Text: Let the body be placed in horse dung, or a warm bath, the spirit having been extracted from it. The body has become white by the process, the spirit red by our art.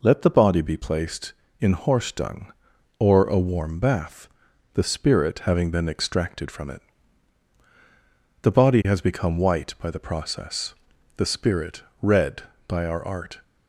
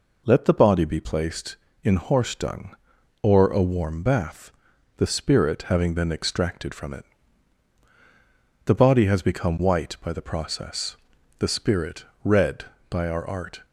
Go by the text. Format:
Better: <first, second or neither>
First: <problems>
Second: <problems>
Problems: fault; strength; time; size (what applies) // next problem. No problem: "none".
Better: neither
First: pauses between "spirit" and "red"; slight; at 11.8 s; 0.18 s long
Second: pauses between "spirit" and "red"; slight; at 12.0 s; 0.18 s long